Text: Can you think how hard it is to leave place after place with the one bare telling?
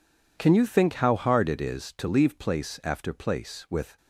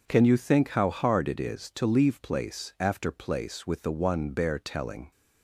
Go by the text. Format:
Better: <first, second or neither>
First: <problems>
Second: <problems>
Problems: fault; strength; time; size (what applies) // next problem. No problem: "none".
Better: second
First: stops before "the one bare telling"; at 3.9 s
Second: none